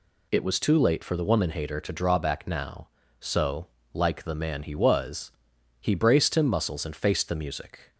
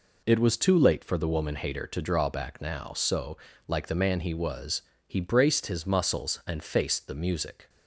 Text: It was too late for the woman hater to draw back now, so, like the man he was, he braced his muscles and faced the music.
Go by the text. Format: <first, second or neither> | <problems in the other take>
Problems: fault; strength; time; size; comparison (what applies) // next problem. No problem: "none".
second | says "him" for "his"; at 6.3 s